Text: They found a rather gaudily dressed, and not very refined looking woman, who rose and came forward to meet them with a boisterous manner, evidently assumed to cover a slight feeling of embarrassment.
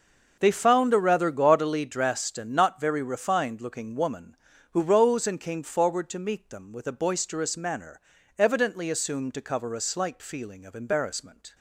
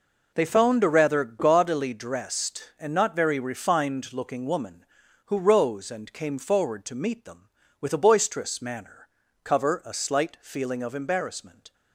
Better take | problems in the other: first | skips "evidently assumed to"; at 9.2 s

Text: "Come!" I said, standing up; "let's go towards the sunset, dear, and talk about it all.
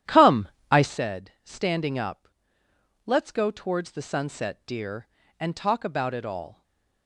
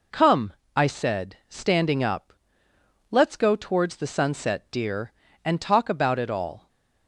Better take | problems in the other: second | starts louder than the rest; strong; until 1.0 s; 11 dB // stays silent after the last word; slight; from 6.5 s on; 0.5 s long

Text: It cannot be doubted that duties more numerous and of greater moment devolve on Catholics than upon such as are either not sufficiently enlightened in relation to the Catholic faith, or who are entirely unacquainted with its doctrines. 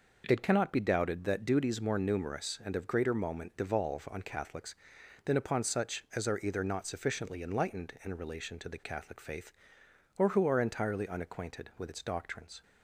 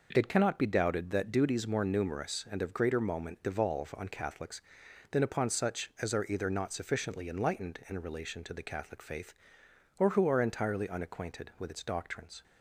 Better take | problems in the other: neither | none

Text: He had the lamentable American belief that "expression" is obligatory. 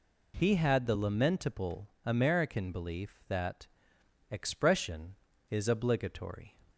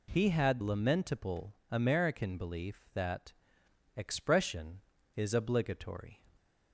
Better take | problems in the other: first | skips "the"; at 0.6 s // pauses between "lamentable" and "American"; slight; at 1.5 s; 0.18 s long; slight in the first // pauses between "that" and "expression"; noticeable; at 3.3 s; 0.64 s long; noticeable in the first

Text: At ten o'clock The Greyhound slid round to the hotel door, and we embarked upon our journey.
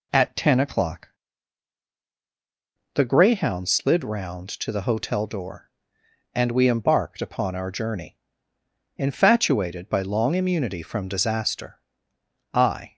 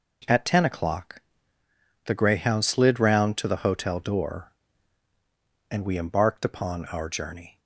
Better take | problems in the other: second | pauses between "o'clock" and "The"; strong; at 1.0 s; 1.8 s long; noticeable in the second // goes on to say "Infatuated by long immunity from disaster I"; strong; from 8.9 s on; 3.9 s long

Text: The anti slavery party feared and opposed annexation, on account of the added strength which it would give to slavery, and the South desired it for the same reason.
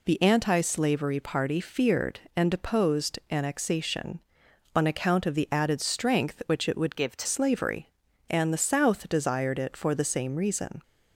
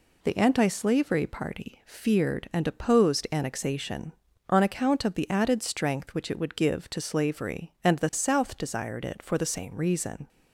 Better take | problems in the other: second | changes voice from "give" to "to"; from 6.9 to 7.2 s; 0.3 s long

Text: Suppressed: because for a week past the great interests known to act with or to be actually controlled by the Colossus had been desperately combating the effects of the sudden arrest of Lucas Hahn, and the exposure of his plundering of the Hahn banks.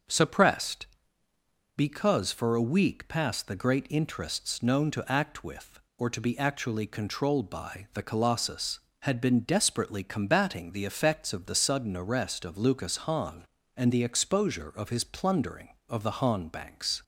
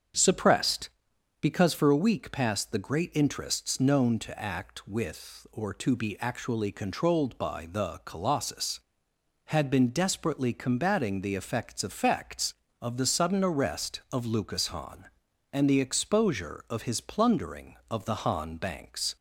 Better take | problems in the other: first | starts louder than the rest; strong; until 1.7 s; 7.5 dB; also in the first // says "effects" twice; at 11.8 s

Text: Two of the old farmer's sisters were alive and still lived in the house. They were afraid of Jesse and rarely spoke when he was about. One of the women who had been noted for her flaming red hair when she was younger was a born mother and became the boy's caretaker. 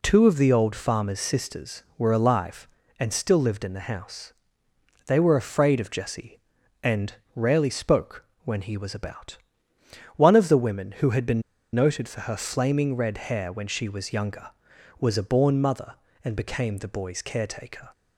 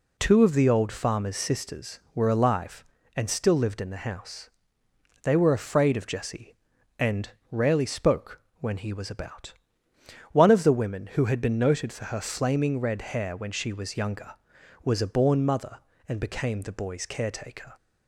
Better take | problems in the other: second | pauses between "and" and "rarely"; slight; at 7.1 s; 0.22 s long; slight in the second // pauses between "spoke" and "when"; slight; at 8.2 s; 0.20 s long; slight in the second // pauses between "been" and "noted"; slight; at 11.4 s; 0.31 s long

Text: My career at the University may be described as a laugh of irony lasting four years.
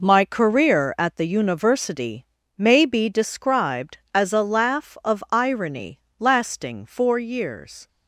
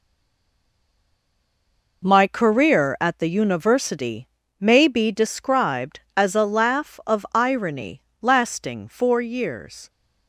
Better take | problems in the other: first | stays silent before the first word; noticeable; until 2.0 s; 2.0 s long // pauses between "University" and "may"; slight; at 4.2 s; 0.32 s long; slight in the first // pauses between "irony" and "lasting"; slight; at 8.0 s; 0.20 s long; slight in the first

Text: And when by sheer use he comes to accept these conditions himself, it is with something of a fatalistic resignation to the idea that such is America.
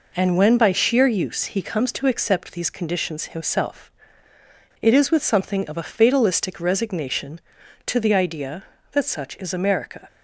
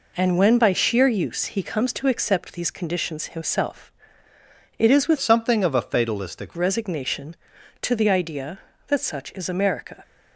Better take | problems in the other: first | changes voice from "something" to "fatalistic"; from 5.1 to 6.5 s; 1.4 s long

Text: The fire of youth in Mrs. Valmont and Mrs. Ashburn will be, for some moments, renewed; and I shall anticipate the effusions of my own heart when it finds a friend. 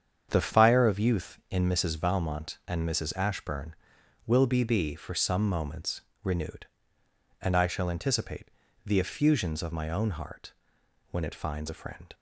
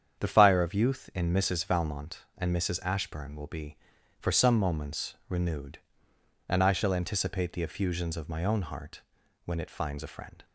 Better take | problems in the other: second | starts louder than the rest; strong; until 1.3 s; 8 dB; strong in the second // says "be" twice; at 4.6 s // pauses between "anticipate" and "the"; at 8.4 s; 0.40 s long // pauses between "heart" and "when"; noticeable; at 10.5 s; 0.58 s long; also in the second

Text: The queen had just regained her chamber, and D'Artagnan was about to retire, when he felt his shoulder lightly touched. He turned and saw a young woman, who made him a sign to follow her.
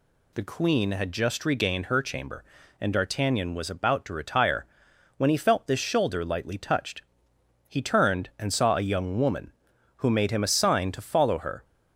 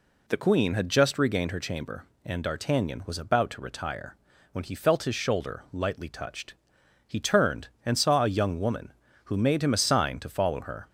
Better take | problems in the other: second | says "this" for "his"; at 5.6 s

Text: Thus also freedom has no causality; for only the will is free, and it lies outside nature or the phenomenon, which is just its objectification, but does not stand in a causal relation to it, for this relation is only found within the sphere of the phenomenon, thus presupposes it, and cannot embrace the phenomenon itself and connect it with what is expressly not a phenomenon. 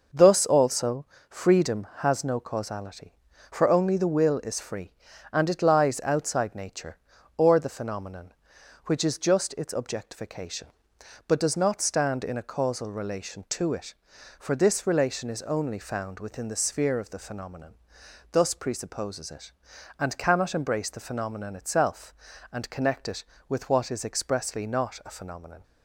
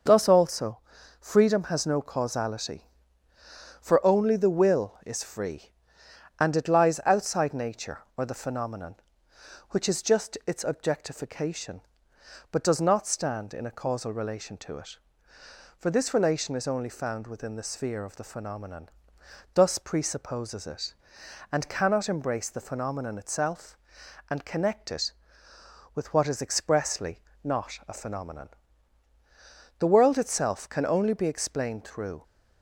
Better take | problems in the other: first | pauses between "also" and "freedom"; at 0.7 s; 0.42 s long; slight in the first // pauses between "expressly" and "not"; slight; at 27.1 s; 0.24 s long // goes on to say "The world itself can only be explained through"; strong; from 29.7 s on; 2.4 s long

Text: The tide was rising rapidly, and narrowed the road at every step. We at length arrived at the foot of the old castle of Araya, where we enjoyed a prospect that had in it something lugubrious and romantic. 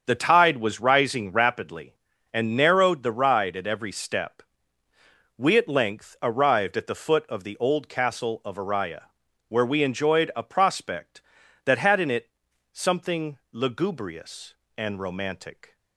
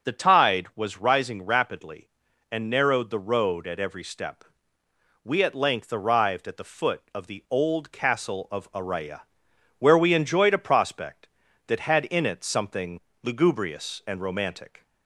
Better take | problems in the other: second | starts louder than the rest; until 1.0 s; 7 dB; also in the second // says "ride" for "road"; at 3.1 s // pauses between "it" and "something"; at 12.2 s; 0.44 s long // pauses between "something" and "lugubrious"; slight; at 13.3 s; 0.16 s long; slight in the second

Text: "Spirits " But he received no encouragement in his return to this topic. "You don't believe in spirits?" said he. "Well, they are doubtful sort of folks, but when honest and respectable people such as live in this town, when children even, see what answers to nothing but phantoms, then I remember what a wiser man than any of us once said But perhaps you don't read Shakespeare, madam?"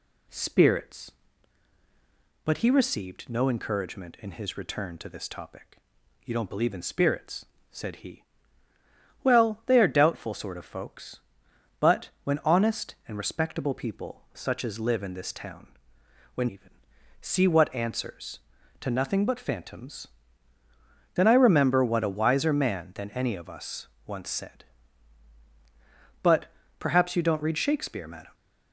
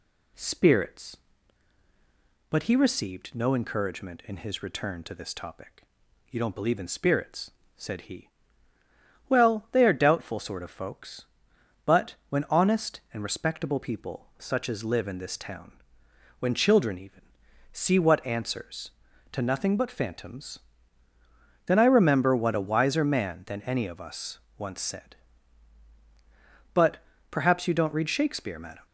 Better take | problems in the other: second | skips "children"; at 16.4 s // pauses between "us" and "once"; slight; at 23.8 s; 0.18 s long; slight in the second // pauses between "But" and "perhaps"; slight; at 26.4 s; 0.32 s long; slight in the second

